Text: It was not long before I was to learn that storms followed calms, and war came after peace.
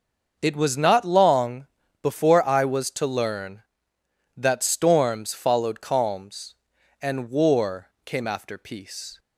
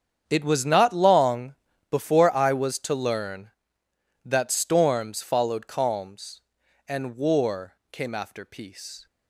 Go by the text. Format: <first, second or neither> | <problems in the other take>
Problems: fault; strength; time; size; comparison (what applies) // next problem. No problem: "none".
first | gets quieter; strong; throughout; 15 dB // starts louder than the rest; strong; until 1.2 s; 8 dB; also in the first // pauses between "long" and "before"; at 1.5 s; 0.38 s long; also in the first // pauses between "war" and "came"; slight; at 7.7 s; 0.16 s long; slight in the first